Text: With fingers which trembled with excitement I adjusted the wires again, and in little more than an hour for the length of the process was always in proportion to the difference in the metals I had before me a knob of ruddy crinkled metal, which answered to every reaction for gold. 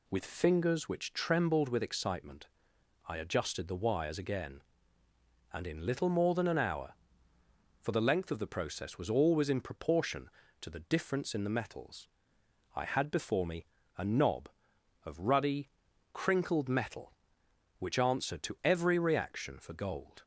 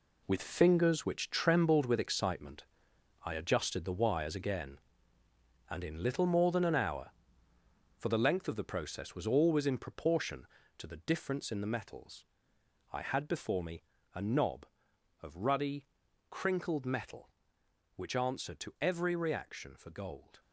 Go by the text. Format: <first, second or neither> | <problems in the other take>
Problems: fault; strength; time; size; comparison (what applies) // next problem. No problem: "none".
first | gets quieter; strong; throughout; 9 dB // pauses between "excitement" and "I"; noticeable; at 2.6 s; 0.62 s long; noticeable in the first // pauses between "metals" and "I"; noticeable; at 12.2 s; 0.70 s long; noticeable in the first // pauses between "me" and "a"; slight; at 13.8 s; 0.32 s long; slight in the first // pauses between "ruddy" and "crinkled"; at 15.8 s; 0.42 s long; also in the first